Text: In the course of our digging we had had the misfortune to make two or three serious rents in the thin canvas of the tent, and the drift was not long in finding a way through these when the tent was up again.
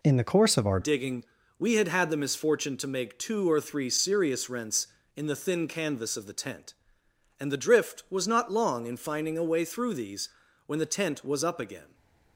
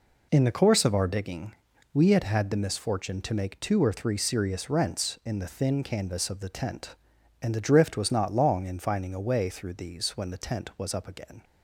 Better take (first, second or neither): second